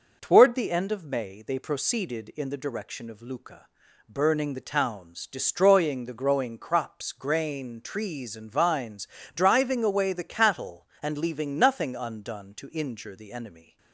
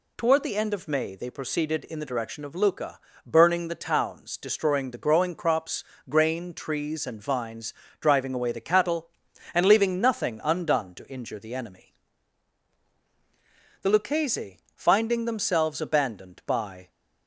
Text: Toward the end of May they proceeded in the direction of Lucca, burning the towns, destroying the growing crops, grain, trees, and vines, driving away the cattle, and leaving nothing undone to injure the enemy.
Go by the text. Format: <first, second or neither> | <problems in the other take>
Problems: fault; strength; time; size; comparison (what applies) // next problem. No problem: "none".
first | goes on to say "The Lucchese finding themselves abandoned by"; strong; from 13.8 s on; 3.0 s long